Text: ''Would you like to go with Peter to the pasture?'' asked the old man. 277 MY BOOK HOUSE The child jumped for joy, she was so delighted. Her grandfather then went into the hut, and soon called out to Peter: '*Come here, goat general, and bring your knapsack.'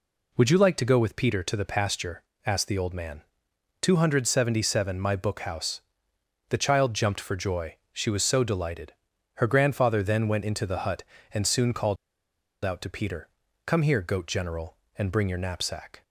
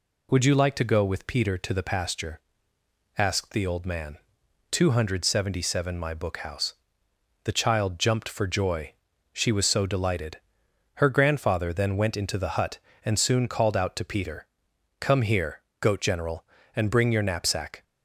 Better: second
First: pauses between "HOUSE" and "The"; noticeable; at 5.8 s; 0.66 s long // pauses between "called" and "out"; noticeable; at 11.9 s; 0.68 s long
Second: pauses between "HOUSE" and "The"; noticeable; at 6.7 s; 0.70 s long

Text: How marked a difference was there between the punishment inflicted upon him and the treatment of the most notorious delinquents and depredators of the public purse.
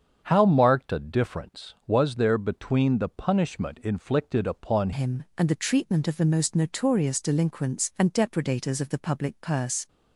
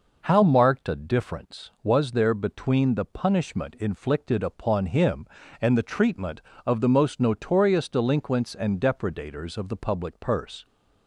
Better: second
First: starts louder than the rest; strong; until 1.2 s; 7.5 dB // changes voice at "him"; from 4.9 s on; 4.9 s long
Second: none

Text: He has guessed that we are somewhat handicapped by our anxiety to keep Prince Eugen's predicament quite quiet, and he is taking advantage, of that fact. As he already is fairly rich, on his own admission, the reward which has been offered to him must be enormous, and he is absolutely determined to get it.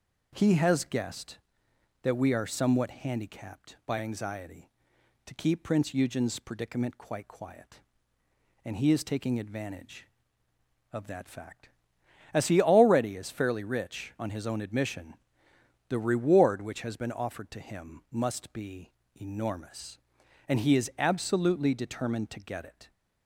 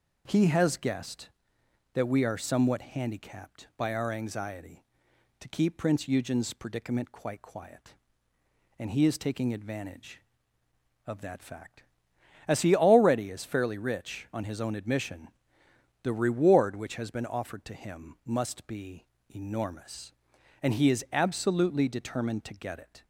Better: second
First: skips "our"; at 3.9 s // pauses between "be" and "enormous"; slight; at 18.9 s; 0.24 s long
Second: pauses between "be" and "enormous"; slight; at 19.0 s; 0.24 s long

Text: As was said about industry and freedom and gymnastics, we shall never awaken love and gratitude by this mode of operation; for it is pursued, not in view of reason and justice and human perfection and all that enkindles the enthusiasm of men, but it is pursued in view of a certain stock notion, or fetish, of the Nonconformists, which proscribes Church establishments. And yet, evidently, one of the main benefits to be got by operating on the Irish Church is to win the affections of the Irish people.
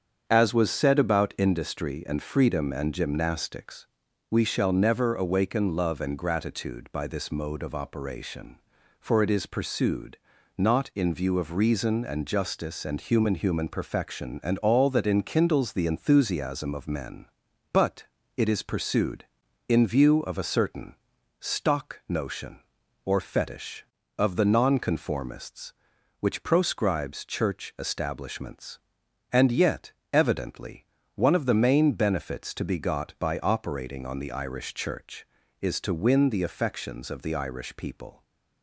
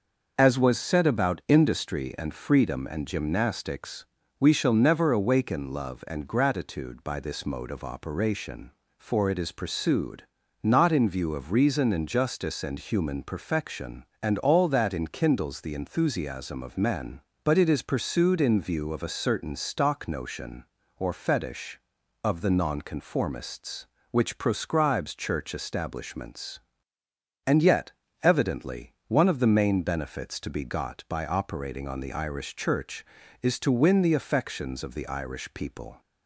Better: second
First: starts louder than the rest; strong; until 1.2 s; 7.5 dB // says "human" twice; at 13.3 s // pauses between "but" and "it"; slight; at 18.0 s; 0.34 s long // pauses between "certain" and "stock"; at 20.9 s; 0.42 s long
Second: starts louder than the rest; noticeable; until 1.3 s; 6 dB

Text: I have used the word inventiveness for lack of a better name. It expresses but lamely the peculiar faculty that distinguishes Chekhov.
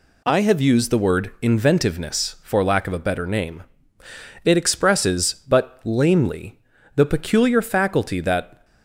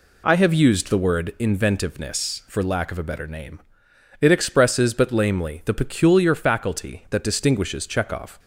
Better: second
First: pauses between "lamely" and "the"; slight; at 6.5 s; 0.36 s long // stops before "distinguishes Chekhov"; at 8.6 s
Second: none

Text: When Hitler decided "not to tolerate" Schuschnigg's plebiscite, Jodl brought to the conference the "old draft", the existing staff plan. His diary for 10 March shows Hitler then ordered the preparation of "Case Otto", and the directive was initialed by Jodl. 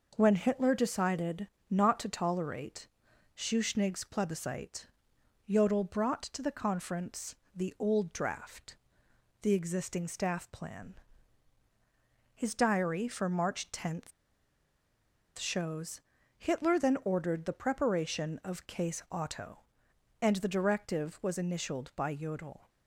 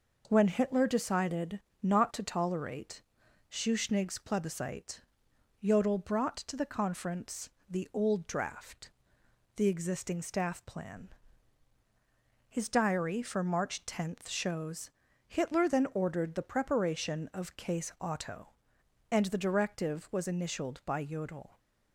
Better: second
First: pauses between "decided" and "not"; slight; at 1.4 s; 0.24 s long // pauses between "tolerate" and "Schuschnigg's"; noticeable; at 2.8 s; 0.48 s long // pauses between "conference" and "the"; slight; at 7.3 s; 0.22 s long // pauses between "March" and "shows"; strong; at 14.1 s; 1.2 s long // pauses between "shows" and "Hitler"; slight; at 16.0 s; 0.36 s long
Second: pauses between "decided" and "not"; slight; at 1.5 s; 0.24 s long // pauses between "tolerate" and "Schuschnigg's"; noticeable; at 3.0 s; 0.48 s long // pauses between "conference" and "the"; slight; at 7.4 s; 0.22 s long // pauses between "shows" and "Hitler"; slight; at 14.8 s; 0.36 s long

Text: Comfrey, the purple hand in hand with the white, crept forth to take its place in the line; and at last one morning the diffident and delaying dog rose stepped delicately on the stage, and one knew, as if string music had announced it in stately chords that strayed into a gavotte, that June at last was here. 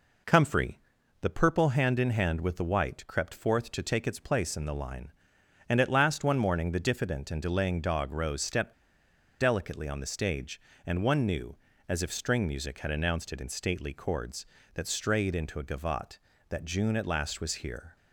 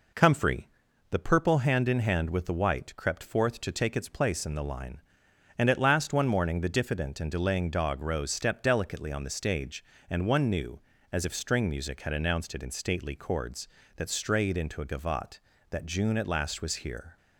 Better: second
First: pauses between "stepped" and "delicately"; noticeable; at 8.7 s; 0.68 s long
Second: none

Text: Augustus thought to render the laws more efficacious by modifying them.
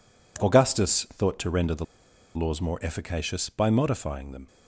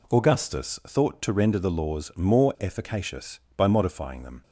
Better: second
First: pauses between "the" and "laws"; noticeable; at 1.8 s; 0.50 s long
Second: none

